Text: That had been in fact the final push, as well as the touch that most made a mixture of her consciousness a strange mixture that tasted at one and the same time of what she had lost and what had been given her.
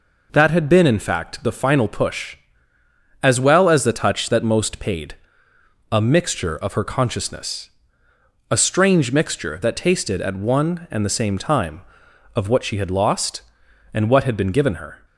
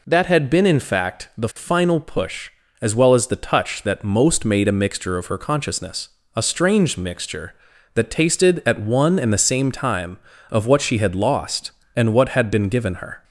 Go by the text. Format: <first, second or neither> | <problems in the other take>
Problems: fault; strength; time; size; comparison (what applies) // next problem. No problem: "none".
second | says "paid" for "made"; at 4.7 s // pauses between "consciousness" and "a"; noticeable; at 7.6 s; 0.80 s long; slight in the second